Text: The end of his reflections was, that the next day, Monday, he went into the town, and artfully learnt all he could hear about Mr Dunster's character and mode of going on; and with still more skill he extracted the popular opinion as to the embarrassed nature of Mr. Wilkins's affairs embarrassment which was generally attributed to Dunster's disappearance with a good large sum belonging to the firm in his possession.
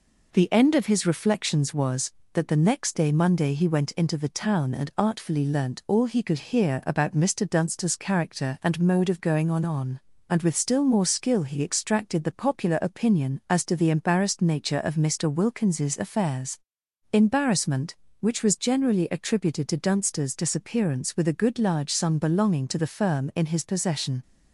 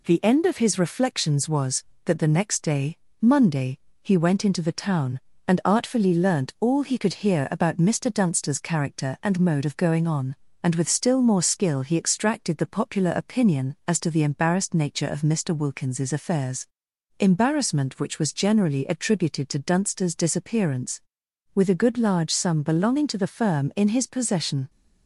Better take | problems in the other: second | says "on" twice; at 9.6 s // pauses between "affairs" and "embarrassment"; noticeable; at 16.5 s; 0.52 s long; noticeable in the second

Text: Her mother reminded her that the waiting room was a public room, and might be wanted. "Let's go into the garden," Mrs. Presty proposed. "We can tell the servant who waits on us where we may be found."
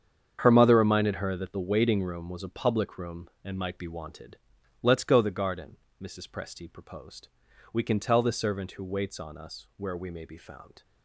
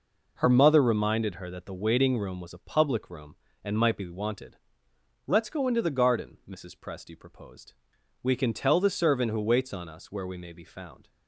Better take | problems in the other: second | starts louder than the rest; strong; until 1.4 s; 8 dB // skips "into"; at 5.1 s

